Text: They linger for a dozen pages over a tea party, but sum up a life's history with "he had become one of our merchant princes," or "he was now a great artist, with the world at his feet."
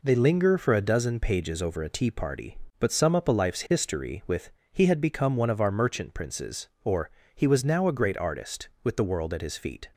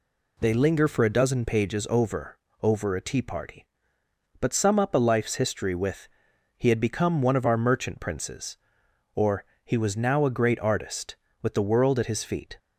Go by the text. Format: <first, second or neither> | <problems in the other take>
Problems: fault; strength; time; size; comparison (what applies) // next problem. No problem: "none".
first | says "over" twice; at 2.6 s // pauses between "with" and "he"; noticeable; at 6.0 s; 0.48 s long; slight in the first // pauses between "or" and "he"; slight; at 9.4 s; 0.20 s long; slight in the first